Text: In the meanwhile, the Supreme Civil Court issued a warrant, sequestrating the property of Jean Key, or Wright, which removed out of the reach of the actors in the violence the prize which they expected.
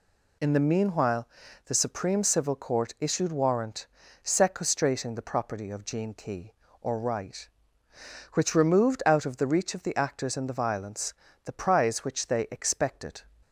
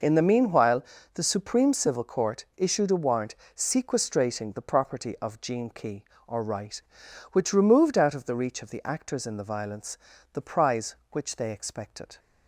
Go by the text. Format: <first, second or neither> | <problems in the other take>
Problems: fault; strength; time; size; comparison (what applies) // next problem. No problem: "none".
second | skips "a"; at 3.3 s // pauses between "violence" and "the"; slight; at 11.1 s; 0.30 s long; slight in the second